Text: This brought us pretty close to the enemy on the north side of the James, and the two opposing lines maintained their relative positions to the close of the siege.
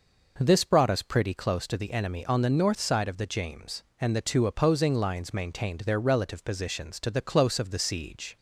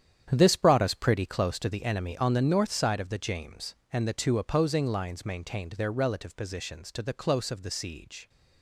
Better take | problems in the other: first | gets quieter; strong; throughout; 11.5 dB

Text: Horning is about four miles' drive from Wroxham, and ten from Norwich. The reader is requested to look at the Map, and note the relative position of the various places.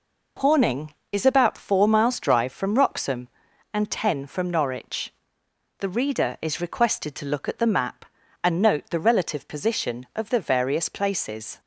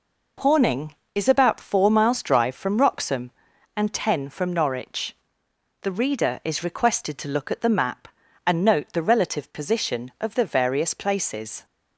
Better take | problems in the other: neither | none

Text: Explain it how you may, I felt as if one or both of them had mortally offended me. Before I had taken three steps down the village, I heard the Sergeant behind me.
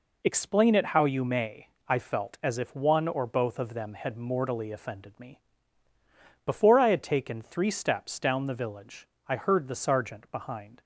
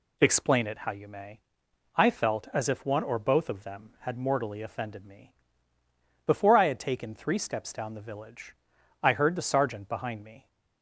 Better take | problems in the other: second | stops before "me"; at 10.8 s

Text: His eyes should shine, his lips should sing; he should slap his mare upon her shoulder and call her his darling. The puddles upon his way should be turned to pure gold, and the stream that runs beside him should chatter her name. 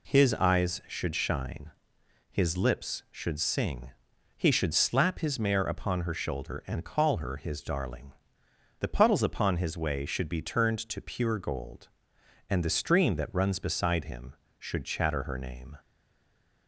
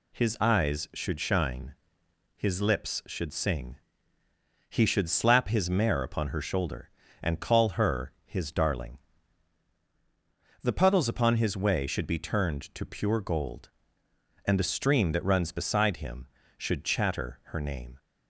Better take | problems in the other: second | stays silent after the last word; slight; from 15.7 s on; 0.9 s long

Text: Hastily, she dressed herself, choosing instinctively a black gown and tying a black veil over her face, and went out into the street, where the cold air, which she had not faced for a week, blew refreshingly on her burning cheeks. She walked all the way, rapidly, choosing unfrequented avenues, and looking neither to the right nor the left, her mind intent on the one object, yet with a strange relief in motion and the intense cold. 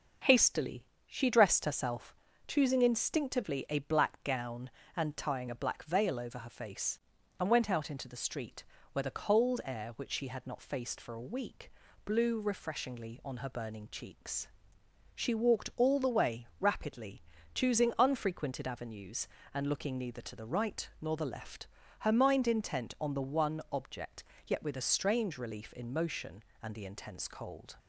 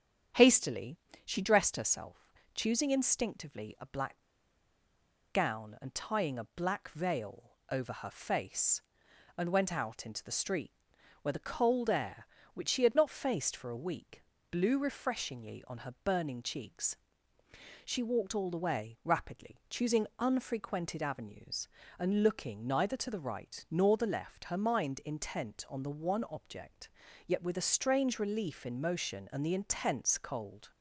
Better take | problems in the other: first | starts louder than the rest; strong; until 1.6 s; 8.5 dB; also in the first // pauses between "black" and "gown"; at 4.1 s; 1.1 s long // pauses between "veil" and "over"; slight; at 7.5 s; 0.18 s long

